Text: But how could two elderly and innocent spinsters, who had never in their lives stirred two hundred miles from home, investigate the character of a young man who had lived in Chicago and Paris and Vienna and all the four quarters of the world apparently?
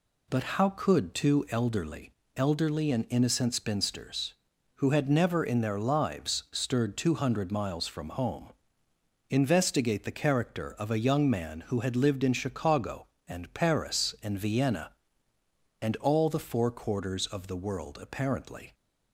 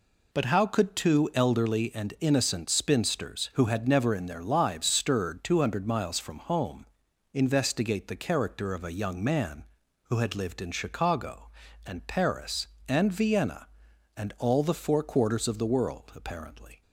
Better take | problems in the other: second | says "elderly" twice; at 2.3 s

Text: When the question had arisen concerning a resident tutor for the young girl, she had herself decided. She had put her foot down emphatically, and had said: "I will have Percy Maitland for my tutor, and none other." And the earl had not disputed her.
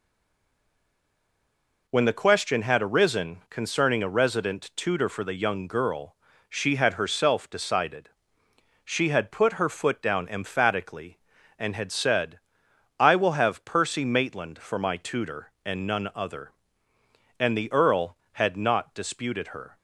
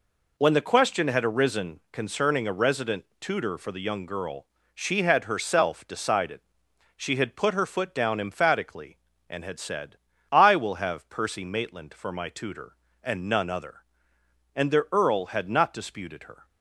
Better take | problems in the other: second | stays silent before the first word; noticeable; until 1.8 s; 1.8 s long

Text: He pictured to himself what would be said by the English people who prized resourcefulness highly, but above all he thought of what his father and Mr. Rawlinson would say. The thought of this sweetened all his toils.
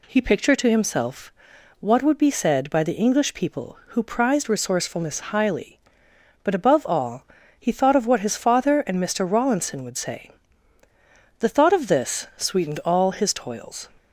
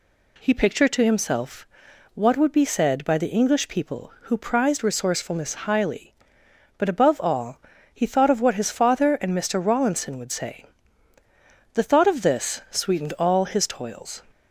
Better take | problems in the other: neither | pauses between "himself" and "what"; noticeable; the same in both // pauses between "all" and "he"; slight; the same in both

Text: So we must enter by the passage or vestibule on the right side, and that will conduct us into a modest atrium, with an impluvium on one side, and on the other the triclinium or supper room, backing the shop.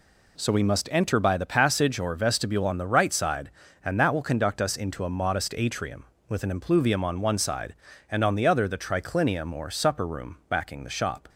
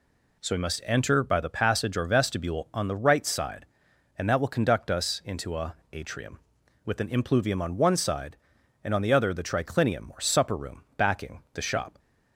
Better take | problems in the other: first | skips "modest"; at 5.8 s

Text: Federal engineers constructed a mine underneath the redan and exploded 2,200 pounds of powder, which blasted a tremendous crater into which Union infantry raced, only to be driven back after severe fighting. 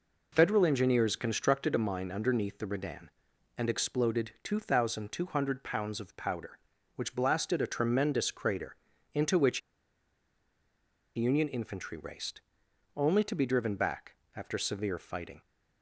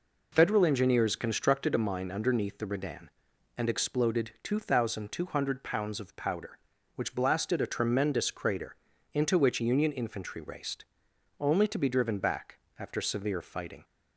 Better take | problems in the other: second | pauses between "crater" and "into"; at 8.7 s; 0.40 s long; also in the second // pauses between "which" and "Union"; strong; at 9.6 s; 1.5 s long // pauses between "back" and "after"; slight; at 14.1 s; 0.20 s long; slight in the second

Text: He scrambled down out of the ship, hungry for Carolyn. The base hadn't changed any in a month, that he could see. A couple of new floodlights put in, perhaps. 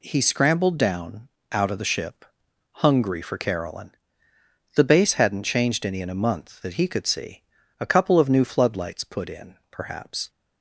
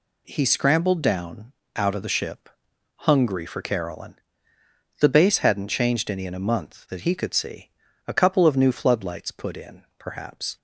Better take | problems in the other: neither | pauses between "down" and "out"; slight; the same in both

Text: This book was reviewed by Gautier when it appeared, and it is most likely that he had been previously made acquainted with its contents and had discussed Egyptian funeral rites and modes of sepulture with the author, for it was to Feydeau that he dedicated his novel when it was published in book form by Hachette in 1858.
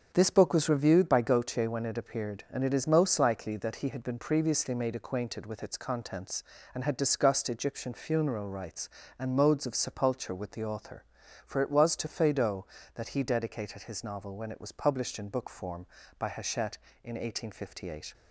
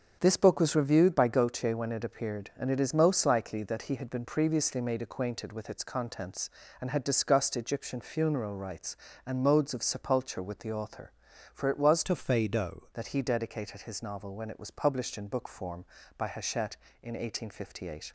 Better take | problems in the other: first | starts louder than the rest; until 1.2 s; 7 dB; also in the first // changes voice from "to" to "Feydeau"; from 12.0 to 12.8 s; 0.8 s long

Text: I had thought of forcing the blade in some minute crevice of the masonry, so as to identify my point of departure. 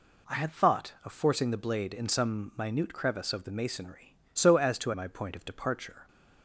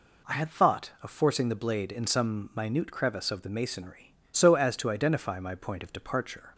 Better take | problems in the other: second | skips "identify"; at 4.9 s

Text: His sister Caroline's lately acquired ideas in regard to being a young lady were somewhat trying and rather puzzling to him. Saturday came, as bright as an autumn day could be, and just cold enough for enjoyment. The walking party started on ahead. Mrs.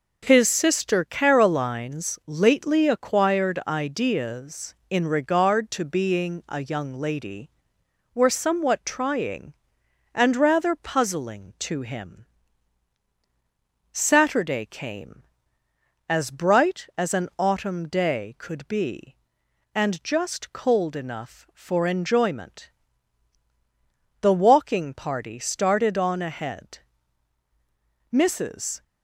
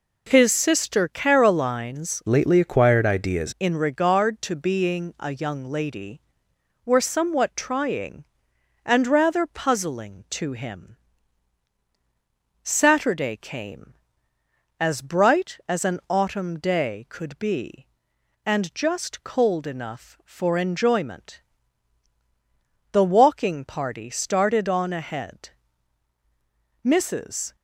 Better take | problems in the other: first | changes voice from "lately" to "ideas"; from 2.2 to 3.5 s; 1.3 s long

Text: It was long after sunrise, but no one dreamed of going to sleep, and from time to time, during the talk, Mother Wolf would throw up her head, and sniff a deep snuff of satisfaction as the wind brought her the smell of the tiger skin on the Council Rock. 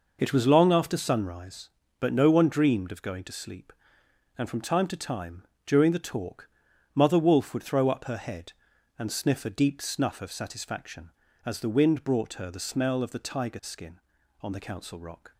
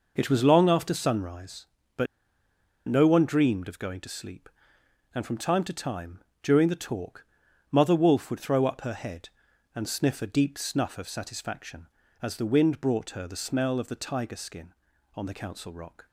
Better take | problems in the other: first | pauses between "but" and "no"; noticeable; at 2.0 s; 0.82 s long

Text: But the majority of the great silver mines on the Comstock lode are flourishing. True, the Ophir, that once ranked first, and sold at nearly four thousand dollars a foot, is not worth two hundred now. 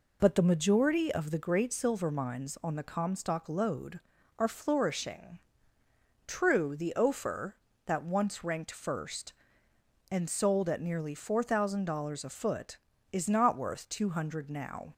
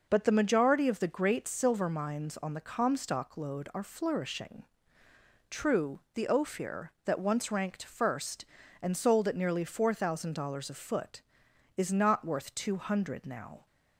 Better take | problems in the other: neither | none

